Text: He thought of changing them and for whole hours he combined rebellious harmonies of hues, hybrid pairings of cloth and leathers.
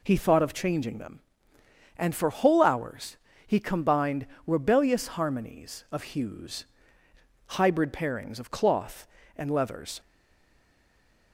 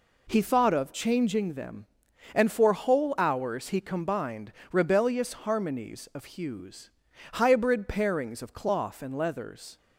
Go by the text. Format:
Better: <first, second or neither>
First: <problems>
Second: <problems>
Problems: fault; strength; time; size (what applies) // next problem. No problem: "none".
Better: second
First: pauses between "hours" and "he"; slight; at 3.1 s; 0.30 s long // pauses between "combined" and "rebellious"; slight; at 4.2 s; 0.22 s long // stays silent after the last word; noticeable; from 10.0 s on; 1.3 s long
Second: pauses between "combined" and "rebellious"; slight; at 4.5 s; 0.22 s long